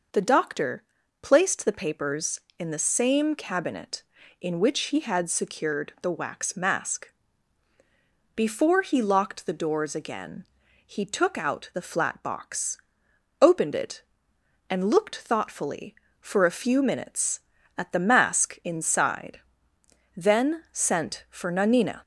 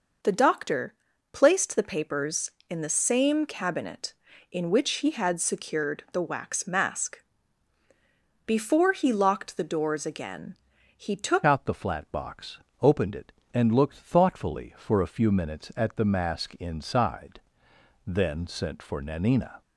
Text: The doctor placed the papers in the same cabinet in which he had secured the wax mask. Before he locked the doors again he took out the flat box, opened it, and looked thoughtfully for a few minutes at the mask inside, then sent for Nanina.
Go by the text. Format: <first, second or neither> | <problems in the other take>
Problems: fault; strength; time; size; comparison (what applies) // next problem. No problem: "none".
first | pauses between "doctor" and "placed"; at 0.9 s; 0.38 s long; also in the first // pauses between "again" and "he"; at 10.5 s; 0.42 s long; also in the first // changes voice at "out"; from 11.4 s on; 8.2 s long